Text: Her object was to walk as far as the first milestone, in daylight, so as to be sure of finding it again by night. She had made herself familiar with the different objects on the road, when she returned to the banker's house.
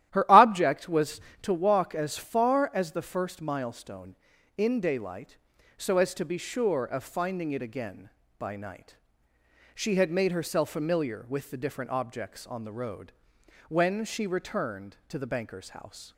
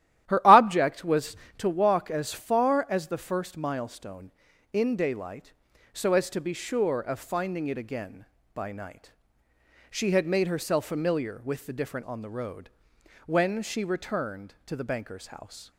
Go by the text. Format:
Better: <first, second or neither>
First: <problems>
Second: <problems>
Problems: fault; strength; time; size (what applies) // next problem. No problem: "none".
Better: first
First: starts louder than the rest; strong; until 1.1 s; 12.5 dB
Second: starts louder than the rest; strong; until 1.3 s; 12.5 dB // skips "objects"; at 12.0 s